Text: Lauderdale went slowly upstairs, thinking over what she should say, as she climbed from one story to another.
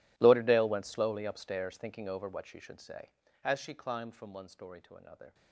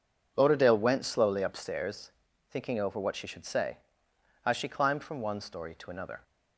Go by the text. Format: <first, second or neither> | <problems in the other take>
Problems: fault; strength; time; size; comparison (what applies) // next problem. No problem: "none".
second | gets quieter; strong; throughout; 21 dB